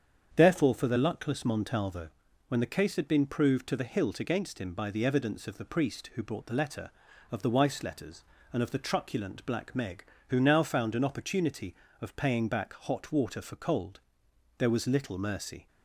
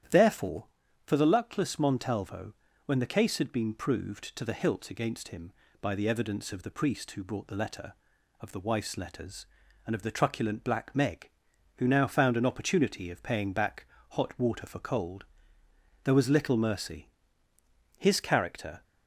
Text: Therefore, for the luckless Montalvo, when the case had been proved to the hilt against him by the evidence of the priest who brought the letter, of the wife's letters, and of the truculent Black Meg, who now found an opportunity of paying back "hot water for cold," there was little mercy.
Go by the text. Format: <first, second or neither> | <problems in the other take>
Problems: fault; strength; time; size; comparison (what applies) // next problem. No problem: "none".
first | starts louder than the rest; strong; until 1.5 s; 10.5 dB; strong in the first // pauses between "back" and "hot"; slight; at 13.8 s; 0.26 s long // goes on to say "His character"; noticeable; from 17.9 s on; 0.88 s long